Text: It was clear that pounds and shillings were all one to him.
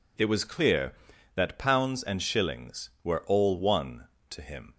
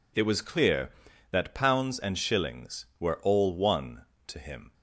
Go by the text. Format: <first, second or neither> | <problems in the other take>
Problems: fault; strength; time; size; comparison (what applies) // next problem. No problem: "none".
neither | none